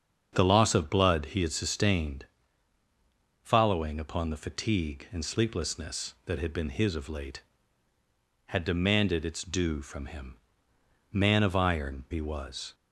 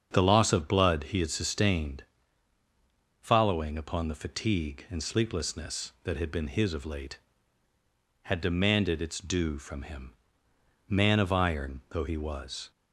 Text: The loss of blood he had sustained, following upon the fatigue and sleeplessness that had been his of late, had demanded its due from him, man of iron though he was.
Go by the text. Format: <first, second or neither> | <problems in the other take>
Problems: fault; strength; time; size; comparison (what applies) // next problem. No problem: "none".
second | starts louder than the rest; strong; until 1.3 s; 7.5 dB; strong in the second // skips "though"; at 12.0 s